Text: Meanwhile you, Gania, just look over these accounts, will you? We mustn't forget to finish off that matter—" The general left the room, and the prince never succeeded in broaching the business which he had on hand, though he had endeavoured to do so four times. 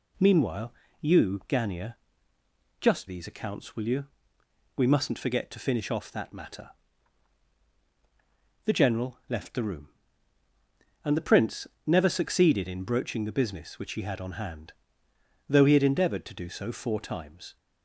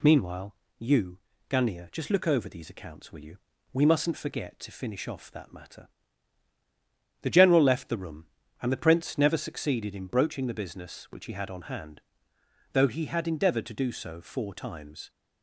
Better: second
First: pauses between "Meanwhile" and "you"; slight; at 0.7 s; 0.28 s long // skips "look over"; at 3.0 s // pauses between "prince" and "never"; slight; at 11.6 s; 0.20 s long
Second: pauses between "Meanwhile" and "you"; slight; at 0.5 s; 0.24 s long

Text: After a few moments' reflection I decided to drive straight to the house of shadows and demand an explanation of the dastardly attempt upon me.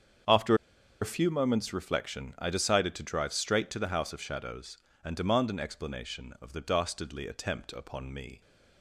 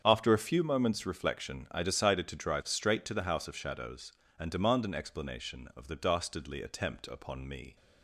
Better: second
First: starts louder than the rest; strong; until 1.7 s; 7 dB // pauses between "After" and "a"; noticeable; at 0.5 s; 0.47 s long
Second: starts louder than the rest; strong; until 1.0 s; 7.5 dB

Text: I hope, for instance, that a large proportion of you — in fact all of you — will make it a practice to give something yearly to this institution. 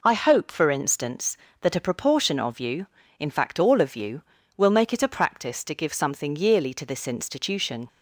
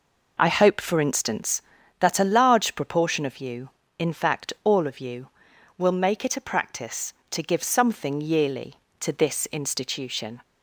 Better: second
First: skips "large"; at 1.7 s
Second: none

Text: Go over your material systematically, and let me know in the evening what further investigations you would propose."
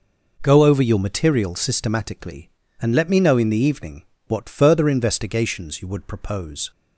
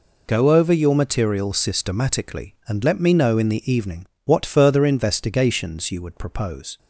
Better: neither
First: pauses between "evening" and "what"; slight; at 4.0 s; 0.24 s long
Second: pauses between "evening" and "what"; slight; at 4.0 s; 0.18 s long

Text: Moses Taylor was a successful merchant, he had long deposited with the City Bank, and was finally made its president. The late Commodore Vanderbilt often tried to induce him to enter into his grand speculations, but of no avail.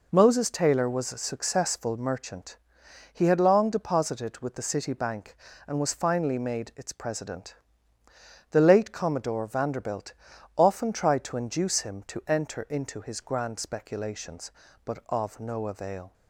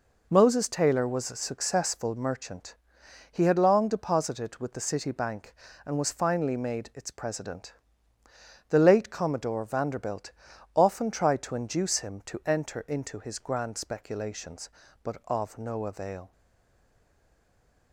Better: first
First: pauses between "Vanderbilt" and "often"; at 10.1 s; 0.44 s long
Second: pauses between "Vanderbilt" and "often"; at 10.3 s; 0.44 s long // stays silent after the last word; noticeable; from 16.3 s on; 1.6 s long

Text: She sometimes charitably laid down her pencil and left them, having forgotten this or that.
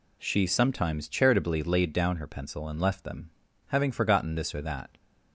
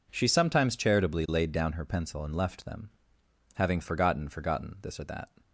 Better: first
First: none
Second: says "forgotten" twice; at 4.2 s

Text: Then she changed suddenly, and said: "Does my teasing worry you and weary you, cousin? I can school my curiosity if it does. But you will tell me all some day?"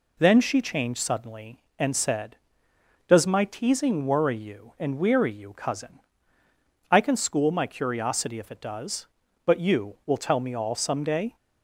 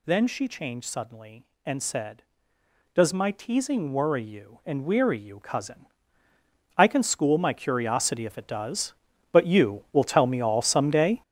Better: first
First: none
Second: gets louder; strong; throughout; 10.5 dB

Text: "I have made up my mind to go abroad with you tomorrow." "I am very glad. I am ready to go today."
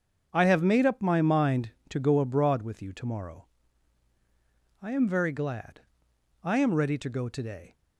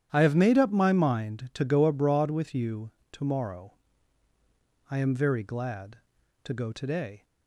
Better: first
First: starts louder than the rest; until 1.3 s; 7 dB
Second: starts louder than the rest; strong; until 1.1 s; 10 dB // pauses between "you" and "tomorrow"; slight; at 2.9 s; 0.20 s long // skips "I am ready"; at 6.2 s

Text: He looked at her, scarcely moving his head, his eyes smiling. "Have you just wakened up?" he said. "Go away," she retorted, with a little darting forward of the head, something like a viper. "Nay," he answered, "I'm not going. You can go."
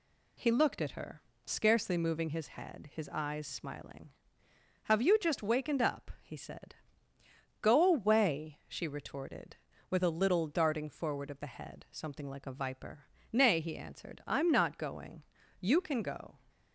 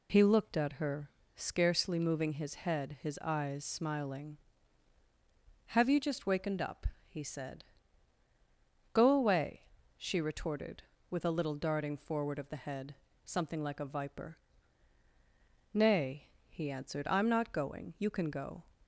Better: neither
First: none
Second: none

